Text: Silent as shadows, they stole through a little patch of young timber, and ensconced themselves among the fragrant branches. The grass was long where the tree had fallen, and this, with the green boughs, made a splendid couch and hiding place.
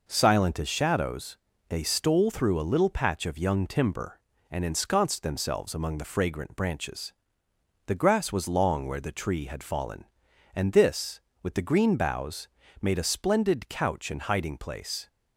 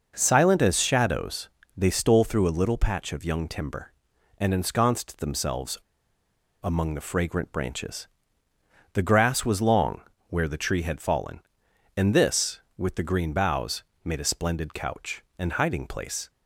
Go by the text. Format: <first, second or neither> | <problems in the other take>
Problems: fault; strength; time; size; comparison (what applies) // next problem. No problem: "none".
first | pauses between "themselves" and "among"; noticeable; at 5.7 s; 0.85 s long // pauses between "long" and "where"; slight; at 10.0 s; 0.26 s long